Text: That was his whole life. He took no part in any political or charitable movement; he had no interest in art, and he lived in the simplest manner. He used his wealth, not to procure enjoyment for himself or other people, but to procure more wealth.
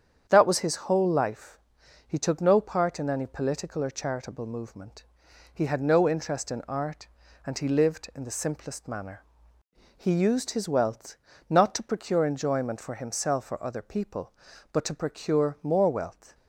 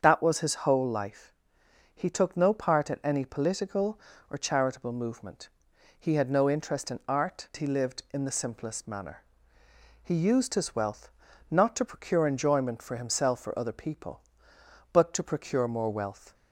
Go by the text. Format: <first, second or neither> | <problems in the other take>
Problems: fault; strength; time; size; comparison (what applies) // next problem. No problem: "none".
first | starts louder than the rest; until 1.0 s; 7 dB; strong in the first // skips "and"; at 7.5 s